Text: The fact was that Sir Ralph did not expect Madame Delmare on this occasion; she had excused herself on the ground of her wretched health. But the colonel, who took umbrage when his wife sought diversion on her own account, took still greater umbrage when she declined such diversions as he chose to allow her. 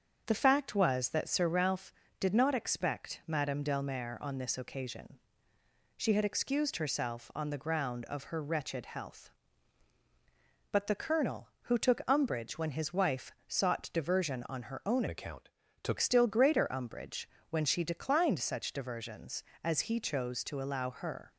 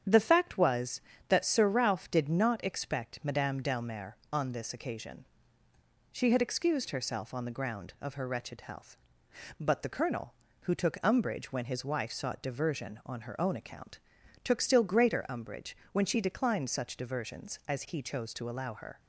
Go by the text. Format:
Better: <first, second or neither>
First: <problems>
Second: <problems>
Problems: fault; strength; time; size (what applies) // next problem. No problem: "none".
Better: second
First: starts louder than the rest; until 1.2 s; 7 dB // changes voice from "account" to "took"; from 15.0 to 15.9 s; 0.9 s long // pauses between "umbrage" and "when"; slight; at 17.2 s; 0.22 s long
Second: starts louder than the rest; strong; until 1.3 s; 8.5 dB // pauses between "umbrage" and "when"; slight; at 15.7 s; 0.20 s long